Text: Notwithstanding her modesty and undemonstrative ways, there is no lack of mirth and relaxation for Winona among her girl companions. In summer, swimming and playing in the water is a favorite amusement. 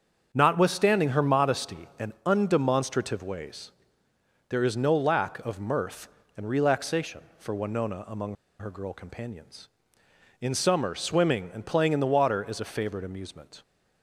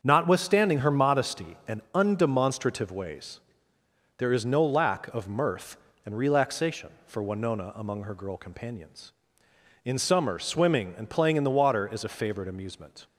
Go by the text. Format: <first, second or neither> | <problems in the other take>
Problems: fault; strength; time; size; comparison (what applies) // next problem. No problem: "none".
second | starts louder than the rest; until 1.3 s; 7 dB; also in the second // pauses between "among" and "her"; slight; at 8.3 s; 0.24 s long